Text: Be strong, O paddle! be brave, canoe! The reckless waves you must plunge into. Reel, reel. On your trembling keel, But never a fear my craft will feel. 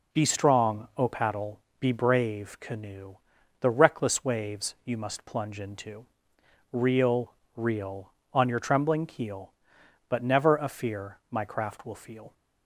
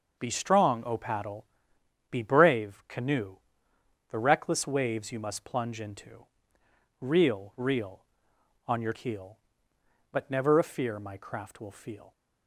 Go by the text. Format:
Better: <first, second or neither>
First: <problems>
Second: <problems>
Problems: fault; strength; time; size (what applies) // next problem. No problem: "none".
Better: first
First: none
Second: starts louder than the rest; noticeable; until 1.2 s; 6 dB // skips "trembling"; at 8.9 s